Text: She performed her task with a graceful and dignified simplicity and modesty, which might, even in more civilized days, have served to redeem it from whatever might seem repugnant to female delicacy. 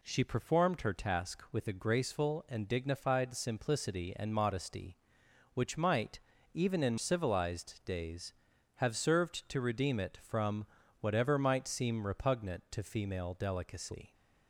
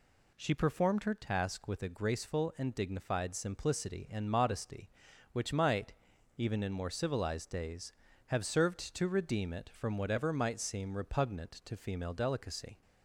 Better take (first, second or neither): second